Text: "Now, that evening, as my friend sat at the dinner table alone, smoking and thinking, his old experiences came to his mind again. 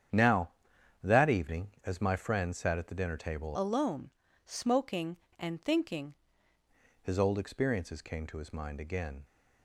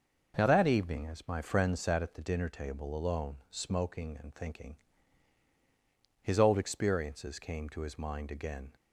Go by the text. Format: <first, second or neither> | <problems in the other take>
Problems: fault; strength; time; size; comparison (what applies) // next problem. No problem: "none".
second | starts louder than the rest; strong; until 1.6 s; 8.5 dB // changes voice from "alone" to "thinking"; from 3.5 to 6.1 s; 2.6 s long